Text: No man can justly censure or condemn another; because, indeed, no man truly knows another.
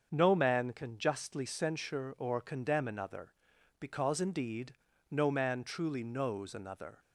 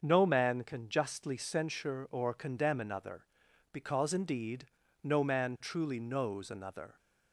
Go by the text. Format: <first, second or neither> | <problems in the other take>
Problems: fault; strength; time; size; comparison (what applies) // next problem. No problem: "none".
neither | starts louder than the rest; the same in both